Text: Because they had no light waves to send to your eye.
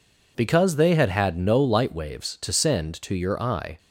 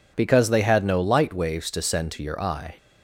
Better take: second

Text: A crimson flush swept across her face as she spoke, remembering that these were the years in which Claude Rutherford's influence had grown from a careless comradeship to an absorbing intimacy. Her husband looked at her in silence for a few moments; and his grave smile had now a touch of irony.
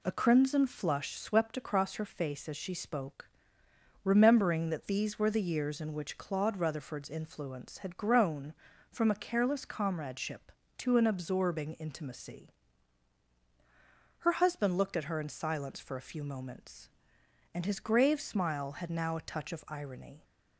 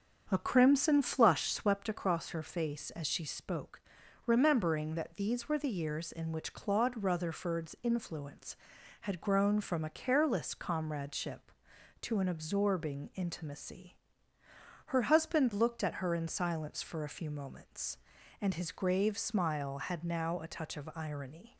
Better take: first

